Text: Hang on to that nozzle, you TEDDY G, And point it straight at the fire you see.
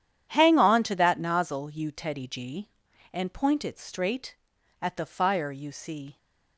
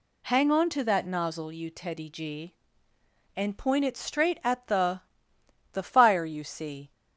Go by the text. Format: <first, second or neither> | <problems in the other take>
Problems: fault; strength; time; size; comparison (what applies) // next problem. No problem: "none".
first | says "the" twice; at 5.7 s